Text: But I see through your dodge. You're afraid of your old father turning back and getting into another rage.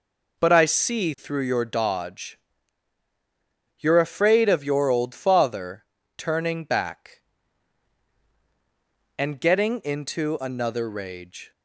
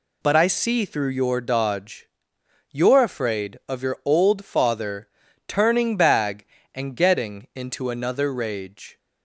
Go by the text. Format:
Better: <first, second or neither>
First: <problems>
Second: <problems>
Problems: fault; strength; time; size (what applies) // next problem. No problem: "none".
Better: first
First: pauses between "father" and "turning"; slight; at 5.8 s; 0.32 s long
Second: pauses between "father" and "turning"; at 5.0 s; 0.38 s long // says "bag" for "back"; at 5.9 s